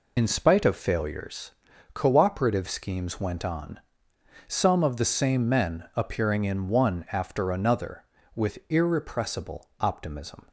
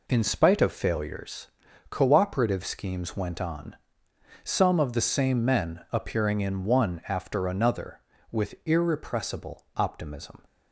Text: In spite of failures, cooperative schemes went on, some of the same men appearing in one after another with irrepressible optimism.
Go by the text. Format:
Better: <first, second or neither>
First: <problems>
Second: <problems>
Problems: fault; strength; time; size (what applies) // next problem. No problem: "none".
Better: second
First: loses the start of "In"; at 0.1 s; 45 ms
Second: none